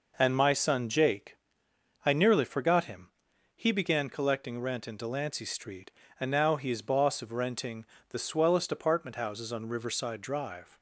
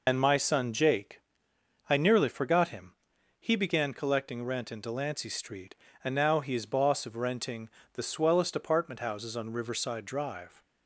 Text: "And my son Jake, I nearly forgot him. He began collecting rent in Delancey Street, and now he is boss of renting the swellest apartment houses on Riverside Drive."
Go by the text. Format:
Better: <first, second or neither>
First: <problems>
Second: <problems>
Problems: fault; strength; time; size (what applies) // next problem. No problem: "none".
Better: first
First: pauses between "renting" and "the"; slight; at 7.8 s; 0.26 s long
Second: loses the start of "And"; at 0.0 s; 95 ms // pauses between "renting" and "the"; slight; at 7.6 s; 0.26 s long